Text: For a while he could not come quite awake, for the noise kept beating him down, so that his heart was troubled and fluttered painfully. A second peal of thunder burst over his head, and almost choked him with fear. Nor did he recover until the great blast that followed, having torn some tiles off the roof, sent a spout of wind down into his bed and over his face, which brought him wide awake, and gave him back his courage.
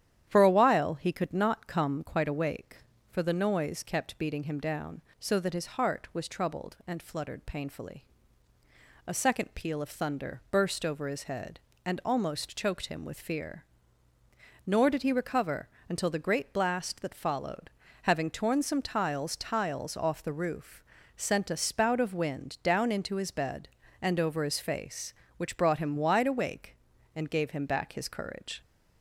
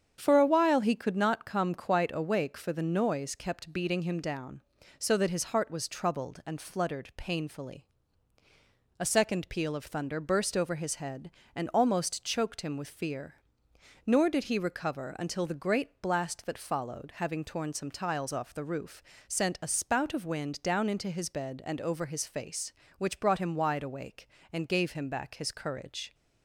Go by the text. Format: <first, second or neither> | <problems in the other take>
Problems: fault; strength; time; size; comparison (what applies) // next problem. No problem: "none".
second | starts louder than the rest; strong; until 1.3 s; 10.5 dB; strong in the second // pauses between "recover" and "until"; slight; at 15.6 s; 0.22 s long // says "tiles" twice; at 19.3 s